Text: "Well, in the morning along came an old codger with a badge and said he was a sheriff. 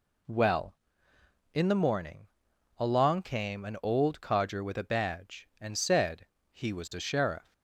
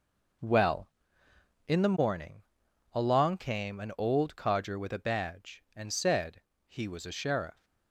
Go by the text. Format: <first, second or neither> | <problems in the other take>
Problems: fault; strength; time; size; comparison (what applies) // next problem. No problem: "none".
first | gets quieter; strong; throughout; 10 dB // pauses between "morning" and "along"; noticeable; at 2.4 s; 0.50 s long; noticeable in the first // pauses between "said" and "he"; slight; at 6.4 s; 0.24 s long; slight in the first